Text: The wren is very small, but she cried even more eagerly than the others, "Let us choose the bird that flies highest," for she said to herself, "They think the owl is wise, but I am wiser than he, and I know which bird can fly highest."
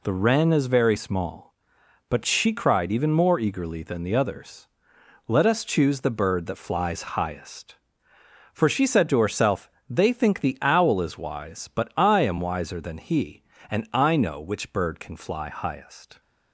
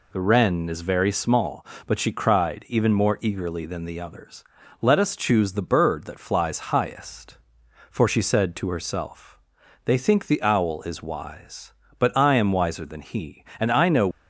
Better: first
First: none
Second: stops before "which bird can fly highest"; at 14.1 s

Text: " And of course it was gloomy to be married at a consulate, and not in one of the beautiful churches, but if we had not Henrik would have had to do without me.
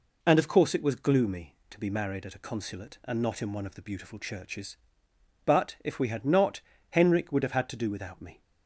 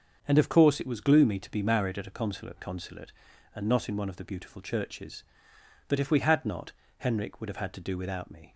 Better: first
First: pauses between "not" and "Henrik"; slight; at 6.5 s; 0.30 s long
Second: starts louder than the rest; until 1.2 s; 6.5 dB // says "consulate" twice; at 2.5 s // pauses between "not" and "Henrik"; slight; at 6.7 s; 0.26 s long

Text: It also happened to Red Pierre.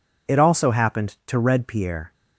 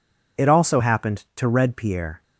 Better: neither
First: none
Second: none

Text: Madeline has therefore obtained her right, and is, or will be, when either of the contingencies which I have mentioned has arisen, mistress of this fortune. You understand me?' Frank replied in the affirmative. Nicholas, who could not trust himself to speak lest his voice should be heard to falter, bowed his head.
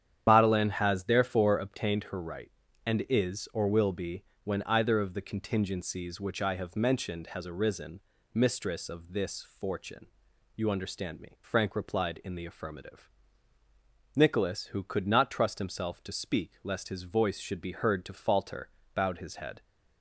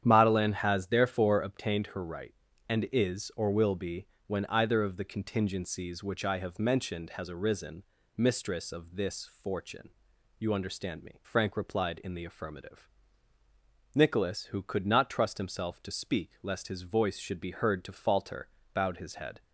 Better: second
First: loses the start of "Madeline"; at 0.2 s; 75 ms // starts louder than the rest; strong; until 1.3 s; 9.5 dB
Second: starts louder than the rest; strong; until 1.0 s; 9.5 dB

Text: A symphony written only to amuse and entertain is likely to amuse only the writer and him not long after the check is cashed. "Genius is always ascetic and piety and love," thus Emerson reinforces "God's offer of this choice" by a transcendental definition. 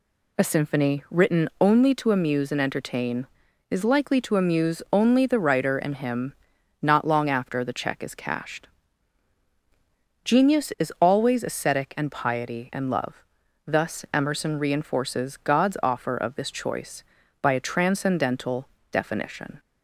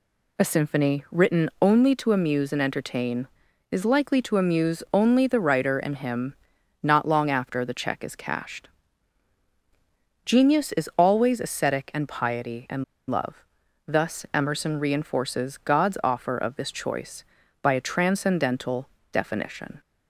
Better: first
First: pauses between "him" and "not"; noticeable; at 6.3 s; 0.48 s long // pauses between "transcendental" and "definition"; slight; at 18.6 s; 0.26 s long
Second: pauses between "him" and "not"; noticeable; at 6.3 s; 0.48 s long // pauses between "and" and "love"; slight; at 12.8 s; 0.25 s long // pauses between "transcendental" and "definition"; slight; at 18.8 s; 0.26 s long

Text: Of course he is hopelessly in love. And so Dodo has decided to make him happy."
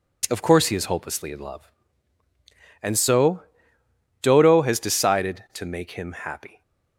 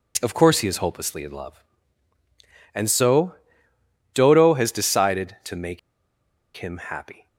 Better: first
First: pauses between "so" and "Dodo"; noticeable; at 3.4 s; 0.80 s long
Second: pauses between "so" and "Dodo"; noticeable; at 3.3 s; 0.80 s long // pauses between "make" and "him"; noticeable; at 5.7 s; 0.77 s long

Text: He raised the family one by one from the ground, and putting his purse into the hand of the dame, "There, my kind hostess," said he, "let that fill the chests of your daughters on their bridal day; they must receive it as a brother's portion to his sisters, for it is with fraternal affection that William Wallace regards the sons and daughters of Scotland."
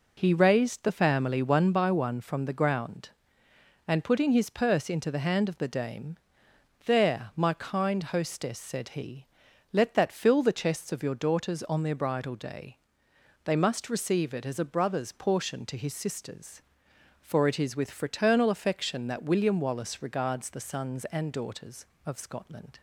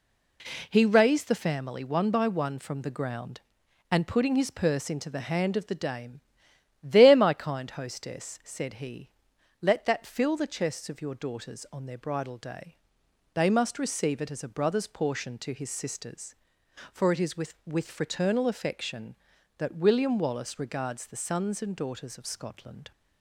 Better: first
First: none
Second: says "with" twice; at 17.6 s

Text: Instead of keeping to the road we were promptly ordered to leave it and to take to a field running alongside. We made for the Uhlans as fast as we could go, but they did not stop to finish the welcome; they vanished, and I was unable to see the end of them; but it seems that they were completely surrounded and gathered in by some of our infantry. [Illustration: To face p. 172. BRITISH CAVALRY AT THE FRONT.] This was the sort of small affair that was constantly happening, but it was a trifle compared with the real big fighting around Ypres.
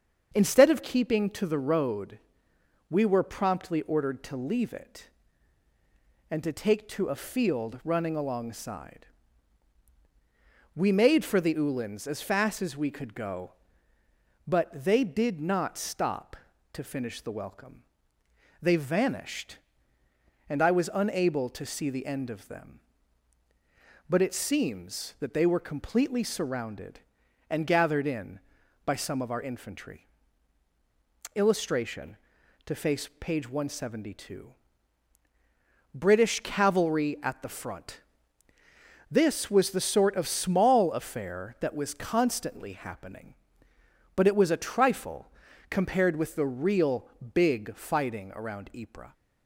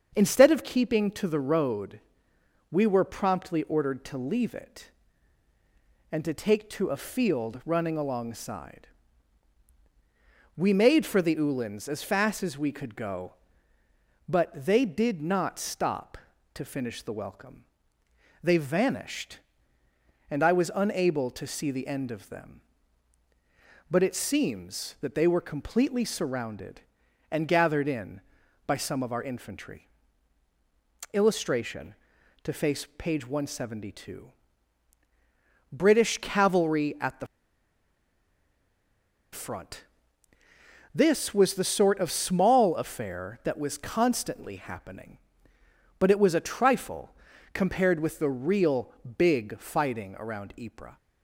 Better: first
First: starts louder than the rest; until 1.3 s; 7 dB // pauses between "road" and "we"; noticeable; at 2.1 s; 0.72 s long // pauses between "trifle" and "compared"; at 45.3 s; 0.38 s long // pauses between "real" and "big"; slight; at 47.0 s; 0.28 s long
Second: starts louder than the rest; until 1.1 s; 7 dB // pauses between "road" and "we"; noticeable; at 2.0 s; 0.72 s long // pauses between "THE" and "FRONT"; strong; at 37.2 s; 2.0 s long // pauses between "trifle" and "compared"; at 47.1 s; 0.38 s long // pauses between "real" and "big"; slight; at 48.9 s; 0.28 s long

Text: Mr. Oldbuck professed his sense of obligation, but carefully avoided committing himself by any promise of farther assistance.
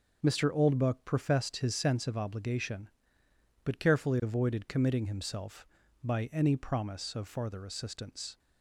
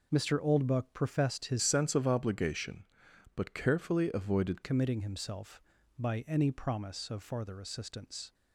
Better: first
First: none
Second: changes voice from "sense" to "avoided"; from 1.6 to 4.6 s; 3.0 s long

